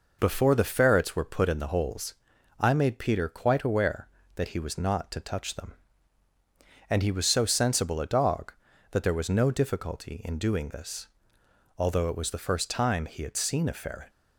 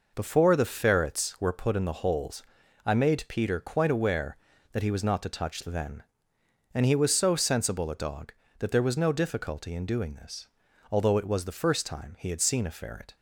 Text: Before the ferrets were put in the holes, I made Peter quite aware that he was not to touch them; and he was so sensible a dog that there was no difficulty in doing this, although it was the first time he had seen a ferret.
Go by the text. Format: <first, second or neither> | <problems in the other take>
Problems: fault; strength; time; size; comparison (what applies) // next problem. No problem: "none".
first | says "then" for "them"; at 5.6 s